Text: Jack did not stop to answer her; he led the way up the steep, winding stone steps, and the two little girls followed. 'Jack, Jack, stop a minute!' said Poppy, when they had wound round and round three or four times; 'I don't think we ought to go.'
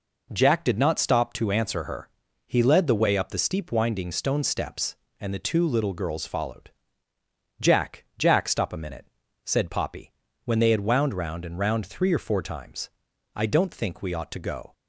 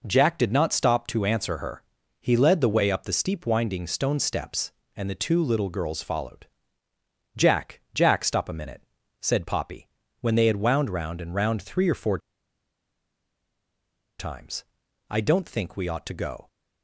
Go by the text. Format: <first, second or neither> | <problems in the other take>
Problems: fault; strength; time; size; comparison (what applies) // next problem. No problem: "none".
first | pauses between "four" and "times"; strong; at 12.1 s; 2.0 s long